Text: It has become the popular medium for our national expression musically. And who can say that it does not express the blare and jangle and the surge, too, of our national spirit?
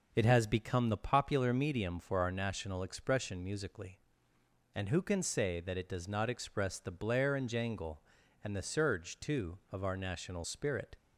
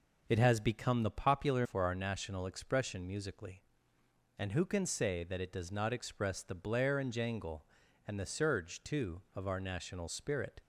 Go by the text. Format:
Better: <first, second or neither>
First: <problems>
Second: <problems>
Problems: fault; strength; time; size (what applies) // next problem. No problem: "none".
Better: first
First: none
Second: skips "medium"; at 1.6 s